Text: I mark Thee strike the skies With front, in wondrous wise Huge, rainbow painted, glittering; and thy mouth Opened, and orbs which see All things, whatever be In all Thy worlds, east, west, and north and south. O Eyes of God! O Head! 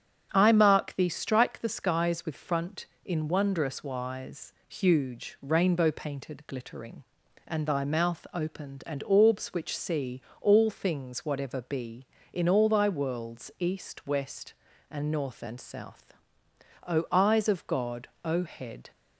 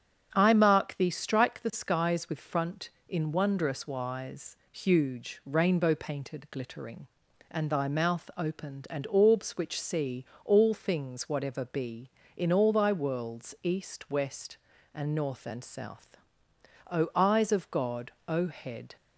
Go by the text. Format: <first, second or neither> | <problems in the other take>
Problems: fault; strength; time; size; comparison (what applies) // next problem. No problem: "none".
neither | starts louder than the rest; strong; the same in both // pauses between "wise" and "Huge"; slight; the same in both // pauses between "see" and "All"; slight; the same in both